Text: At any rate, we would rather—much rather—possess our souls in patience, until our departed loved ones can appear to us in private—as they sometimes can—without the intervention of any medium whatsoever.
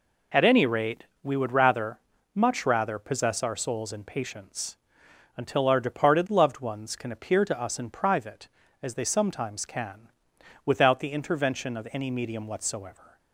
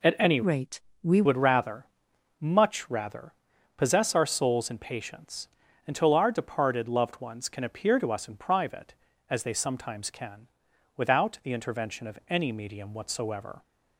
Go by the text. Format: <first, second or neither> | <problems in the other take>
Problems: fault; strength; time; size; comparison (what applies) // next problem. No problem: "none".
first | changes voice from "rate" to "we"; from 0.4 to 1.2 s; 0.8 s long